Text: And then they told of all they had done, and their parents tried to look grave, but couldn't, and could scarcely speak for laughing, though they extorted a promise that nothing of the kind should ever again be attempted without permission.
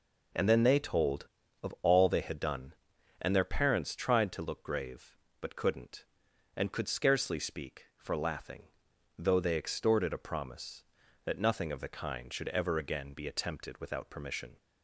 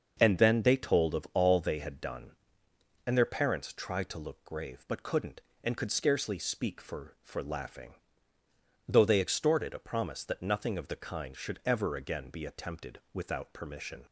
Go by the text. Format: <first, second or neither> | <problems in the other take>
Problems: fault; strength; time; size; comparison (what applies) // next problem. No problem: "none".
first | starts louder than the rest; until 1.2 s; 6.5 dB // says "for" twice; at 7.2 s